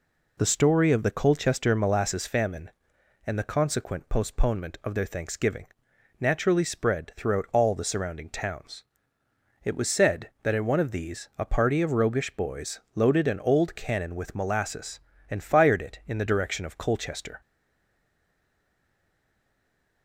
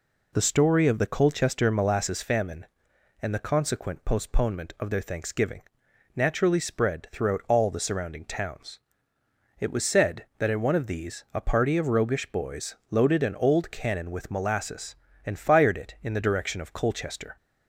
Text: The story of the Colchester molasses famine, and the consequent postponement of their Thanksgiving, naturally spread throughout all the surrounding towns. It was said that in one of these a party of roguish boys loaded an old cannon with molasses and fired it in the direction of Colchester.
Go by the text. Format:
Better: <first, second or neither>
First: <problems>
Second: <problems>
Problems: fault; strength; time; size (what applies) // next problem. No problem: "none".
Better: second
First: pauses between "boys" and "loaded"; slight; at 12.7 s; 0.16 s long // stays silent after the last word; strong; from 17.4 s on; 2.6 s long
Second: pauses between "boys" and "loaded"; slight; at 12.7 s; 0.16 s long